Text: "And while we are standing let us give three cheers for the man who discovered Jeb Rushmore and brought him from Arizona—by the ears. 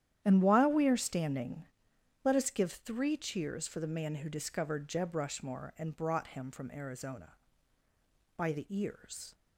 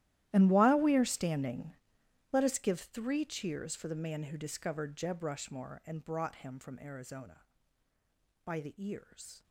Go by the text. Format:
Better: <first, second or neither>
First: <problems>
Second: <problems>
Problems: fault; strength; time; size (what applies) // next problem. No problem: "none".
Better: first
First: starts louder than the rest; strong; until 1.2 s; 10.5 dB // pauses between "standing" and "let"; noticeable; at 1.6 s; 0.60 s long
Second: gets quieter; strong; throughout; 20 dB // starts louder than the rest; strong; until 1.3 s; 13.5 dB // pauses between "standing" and "let"; noticeable; at 1.7 s; 0.60 s long